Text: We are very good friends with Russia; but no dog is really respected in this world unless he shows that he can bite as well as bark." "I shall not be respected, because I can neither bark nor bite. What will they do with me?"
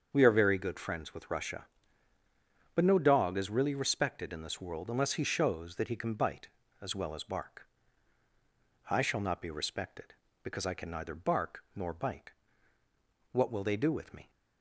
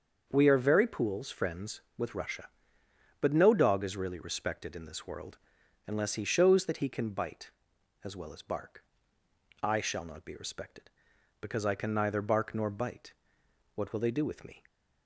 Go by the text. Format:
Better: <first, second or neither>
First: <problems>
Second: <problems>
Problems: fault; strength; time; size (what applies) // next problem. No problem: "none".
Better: first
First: starts louder than the rest; until 1.1 s; 7 dB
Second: starts louder than the rest; until 1.3 s; 7 dB // says "pools" for "good"; at 0.8 s // pauses between "world" and "unless"; noticeable; at 5.3 s; 0.48 s long